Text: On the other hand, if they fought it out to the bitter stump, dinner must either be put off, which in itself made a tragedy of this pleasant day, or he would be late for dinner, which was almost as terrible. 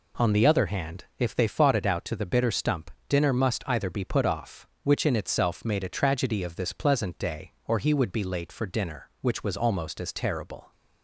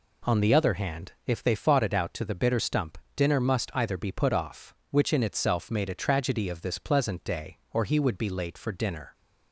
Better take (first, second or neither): first